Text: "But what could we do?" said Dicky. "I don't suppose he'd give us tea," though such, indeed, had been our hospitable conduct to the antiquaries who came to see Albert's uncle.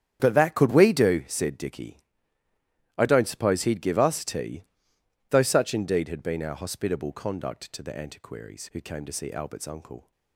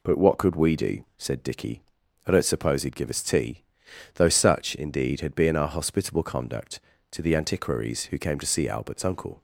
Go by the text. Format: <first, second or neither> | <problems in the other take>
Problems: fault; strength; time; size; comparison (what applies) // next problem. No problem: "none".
second | starts louder than the rest; strong; until 1.2 s; 9.5 dB // says "that" for "what"; at 0.3 s